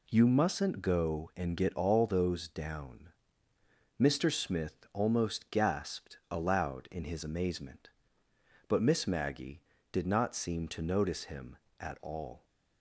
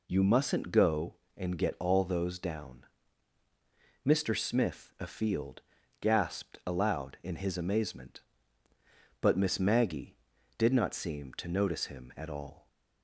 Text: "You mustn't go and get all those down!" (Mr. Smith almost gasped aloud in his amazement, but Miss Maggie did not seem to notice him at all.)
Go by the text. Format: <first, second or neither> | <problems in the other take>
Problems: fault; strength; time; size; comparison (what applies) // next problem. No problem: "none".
first | says "afield" for "almost"; at 4.9 s